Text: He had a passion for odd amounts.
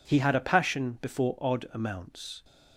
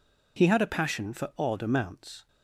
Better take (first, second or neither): second